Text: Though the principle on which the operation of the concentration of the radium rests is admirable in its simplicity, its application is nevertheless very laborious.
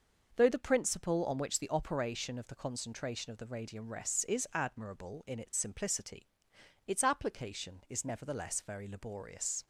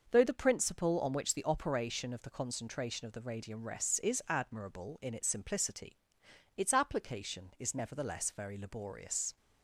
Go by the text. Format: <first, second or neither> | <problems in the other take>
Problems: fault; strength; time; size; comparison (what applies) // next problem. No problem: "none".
neither | starts louder than the rest; noticeable; the same in both